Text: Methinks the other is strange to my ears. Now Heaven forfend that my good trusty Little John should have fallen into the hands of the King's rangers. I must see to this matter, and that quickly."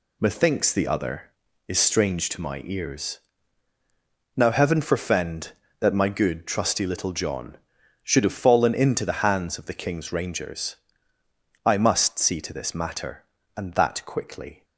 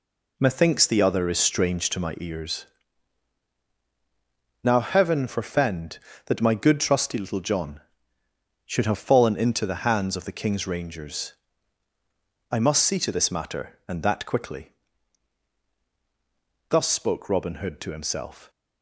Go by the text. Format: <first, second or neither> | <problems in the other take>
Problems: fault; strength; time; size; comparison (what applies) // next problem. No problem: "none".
first | goes on to say "Thus spoke Robin Hood to himself"; strong; from 16.6 s on; 1.8 s long